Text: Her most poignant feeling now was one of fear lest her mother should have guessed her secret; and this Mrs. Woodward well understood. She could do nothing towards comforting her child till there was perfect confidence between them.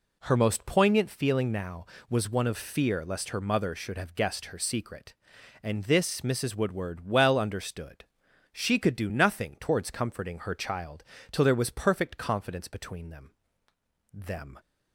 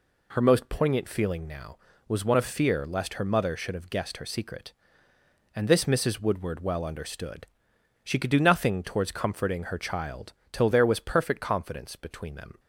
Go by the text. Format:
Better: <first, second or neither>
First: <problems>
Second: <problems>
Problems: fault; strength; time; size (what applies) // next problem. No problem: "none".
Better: second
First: pauses between "child" and "till"; slight; at 11.0 s; 0.29 s long // says "them" twice; at 14.1 s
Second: pauses between "child" and "till"; slight; at 10.3 s; 0.20 s long